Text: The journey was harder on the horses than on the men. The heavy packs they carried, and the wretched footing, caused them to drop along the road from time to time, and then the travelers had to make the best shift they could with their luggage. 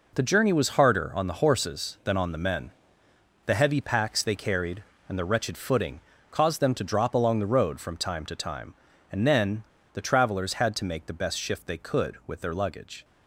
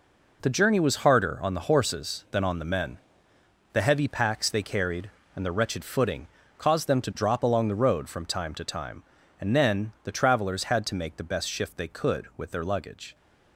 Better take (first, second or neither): second